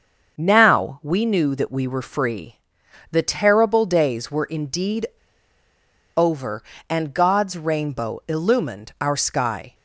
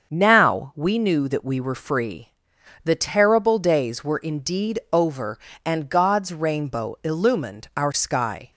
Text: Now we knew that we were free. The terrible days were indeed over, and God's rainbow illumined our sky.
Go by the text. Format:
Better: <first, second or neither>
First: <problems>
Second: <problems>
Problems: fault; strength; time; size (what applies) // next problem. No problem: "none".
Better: second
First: starts louder than the rest; until 1.3 s; 6.5 dB // pauses between "indeed" and "over"; at 5.0 s; 1.0 s long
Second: starts louder than the rest; until 1.1 s; 6.5 dB